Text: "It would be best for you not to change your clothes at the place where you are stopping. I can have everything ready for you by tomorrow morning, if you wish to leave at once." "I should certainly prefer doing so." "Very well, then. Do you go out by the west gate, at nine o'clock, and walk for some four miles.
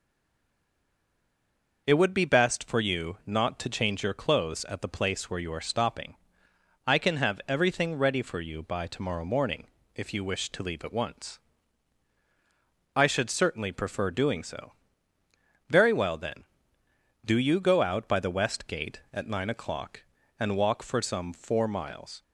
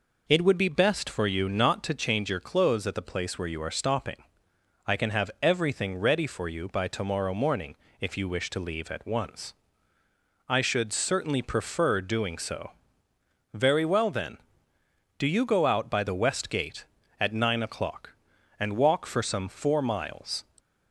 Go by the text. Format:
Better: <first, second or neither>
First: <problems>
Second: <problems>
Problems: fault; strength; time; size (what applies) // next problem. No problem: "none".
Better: second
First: stays silent before the first word; noticeable; until 1.8 s; 1.8 s long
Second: none